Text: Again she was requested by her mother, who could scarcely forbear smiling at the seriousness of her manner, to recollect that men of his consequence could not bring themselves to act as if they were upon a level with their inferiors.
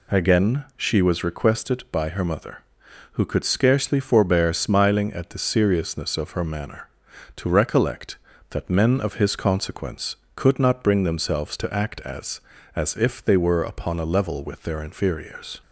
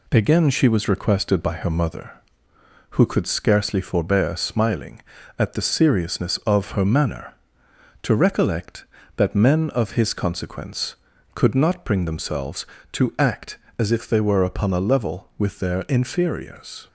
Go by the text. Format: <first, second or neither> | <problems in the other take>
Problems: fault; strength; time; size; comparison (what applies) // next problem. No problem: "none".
second | says "as" twice; at 12.7 s